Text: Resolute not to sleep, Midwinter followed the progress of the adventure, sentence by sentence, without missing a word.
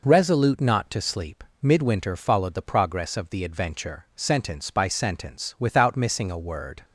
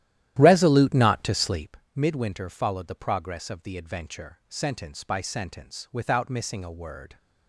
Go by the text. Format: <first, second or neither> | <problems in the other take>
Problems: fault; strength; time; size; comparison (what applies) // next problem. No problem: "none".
first | starts louder than the rest; strong; until 1.8 s; 12.5 dB